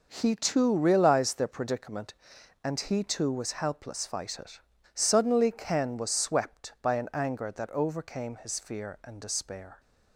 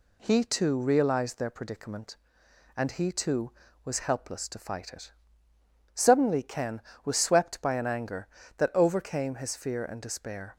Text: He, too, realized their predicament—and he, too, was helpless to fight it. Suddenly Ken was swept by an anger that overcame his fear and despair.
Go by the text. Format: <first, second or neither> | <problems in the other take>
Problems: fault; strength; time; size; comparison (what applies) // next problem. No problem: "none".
second | skips "to"; at 4.0 s